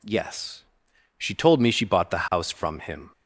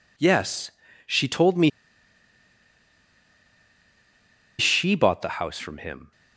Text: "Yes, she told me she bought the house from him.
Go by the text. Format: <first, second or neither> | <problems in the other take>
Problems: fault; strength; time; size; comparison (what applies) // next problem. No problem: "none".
first | pauses between "me" and "she"; strong; at 1.6 s; 2.9 s long